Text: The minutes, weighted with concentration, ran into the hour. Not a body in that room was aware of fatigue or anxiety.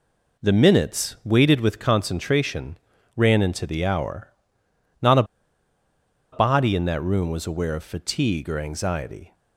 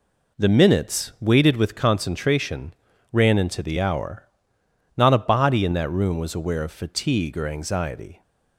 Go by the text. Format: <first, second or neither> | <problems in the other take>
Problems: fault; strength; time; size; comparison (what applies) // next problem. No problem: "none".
second | pauses between "a" and "body"; at 5.2 s; 1.0 s long